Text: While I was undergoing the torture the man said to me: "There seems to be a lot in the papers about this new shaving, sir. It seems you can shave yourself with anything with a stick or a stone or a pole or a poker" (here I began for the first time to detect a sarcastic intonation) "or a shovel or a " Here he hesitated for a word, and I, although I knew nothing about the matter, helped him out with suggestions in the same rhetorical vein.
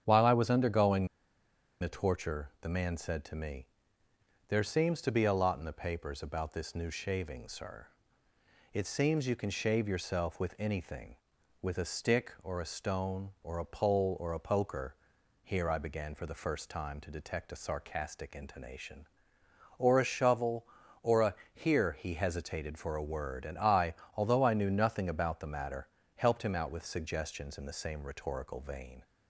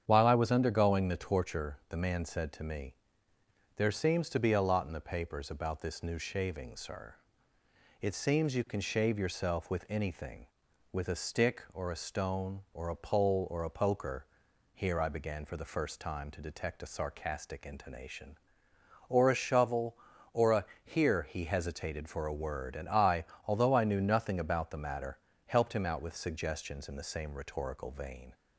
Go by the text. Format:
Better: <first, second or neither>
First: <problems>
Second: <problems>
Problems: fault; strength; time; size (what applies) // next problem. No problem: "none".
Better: second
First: starts louder than the rest; strong; until 1.0 s; 8.5 dB // pauses between "undergoing" and "the"; noticeable; at 1.0 s; 0.74 s long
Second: starts louder than the rest; strong; until 1.0 s; 8.5 dB